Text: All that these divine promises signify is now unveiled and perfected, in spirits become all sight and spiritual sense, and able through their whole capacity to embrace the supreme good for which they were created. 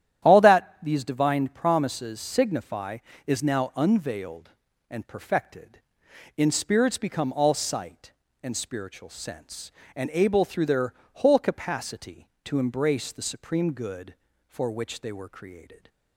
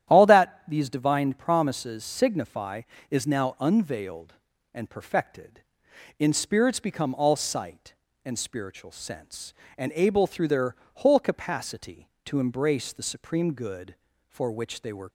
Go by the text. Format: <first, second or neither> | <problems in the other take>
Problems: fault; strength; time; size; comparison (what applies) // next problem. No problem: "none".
first | starts louder than the rest; strong; until 1.1 s; 11.5 dB; strong in the first // pauses between "their" and "whole"; slight; at 10.7 s; 0.20 s long; slight in the first // stops before "created"; at 15.0 s